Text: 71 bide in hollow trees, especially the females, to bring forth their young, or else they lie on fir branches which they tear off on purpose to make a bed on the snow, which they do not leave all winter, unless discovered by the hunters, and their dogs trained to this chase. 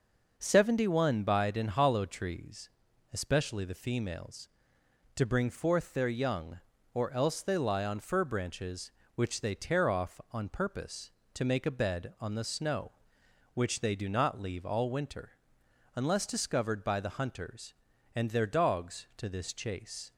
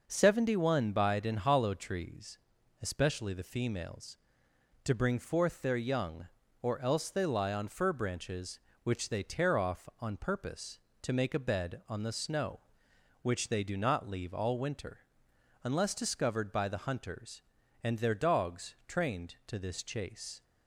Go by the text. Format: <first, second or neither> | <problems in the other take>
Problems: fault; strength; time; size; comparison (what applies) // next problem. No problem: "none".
second | skips "trained"; at 19.1 s